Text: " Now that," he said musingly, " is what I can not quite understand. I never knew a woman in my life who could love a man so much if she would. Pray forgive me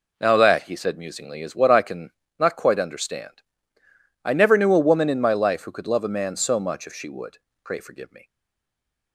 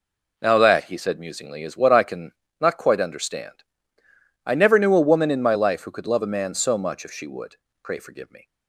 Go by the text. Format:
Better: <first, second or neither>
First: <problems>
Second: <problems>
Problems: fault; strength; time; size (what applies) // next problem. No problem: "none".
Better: second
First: pauses between "can" and "not"; slight; at 2.0 s; 0.30 s long // stays silent after the last word; slight; from 8.2 s on; 0.9 s long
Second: pauses between "can" and "not"; slight; at 2.3 s; 0.30 s long